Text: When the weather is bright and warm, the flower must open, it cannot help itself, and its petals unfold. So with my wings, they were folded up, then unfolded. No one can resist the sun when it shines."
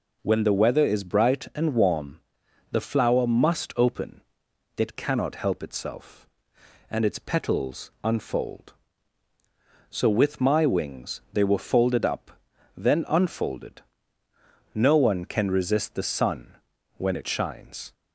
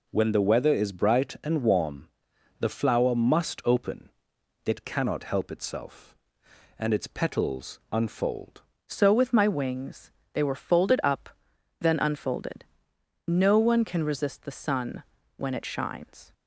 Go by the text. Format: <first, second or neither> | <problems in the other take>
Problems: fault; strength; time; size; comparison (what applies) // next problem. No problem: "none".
first | changes voice at "So"; from 8.8 s on; 7.5 s long // pauses between "sun" and "when"; slight; at 15.0 s; 0.34 s long; also in the first